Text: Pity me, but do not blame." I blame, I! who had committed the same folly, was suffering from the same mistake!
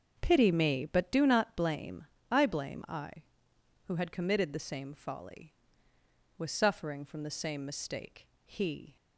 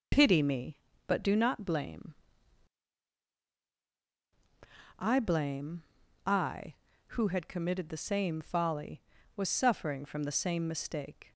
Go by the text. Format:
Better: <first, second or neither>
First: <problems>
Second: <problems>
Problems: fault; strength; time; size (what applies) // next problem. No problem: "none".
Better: second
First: starts louder than the rest; until 1.2 s; 6.5 dB // goes on to say "He"; from 8.4 s on; 0.50 s long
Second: none